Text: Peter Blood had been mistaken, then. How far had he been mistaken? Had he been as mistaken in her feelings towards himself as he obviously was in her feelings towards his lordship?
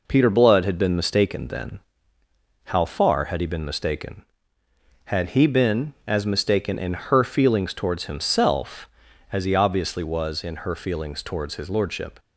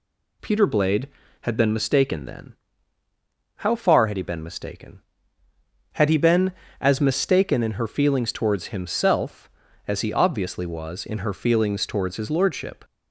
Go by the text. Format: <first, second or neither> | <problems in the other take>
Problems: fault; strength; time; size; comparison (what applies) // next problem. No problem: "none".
first | says "Blade" for "Blood"; at 0.6 s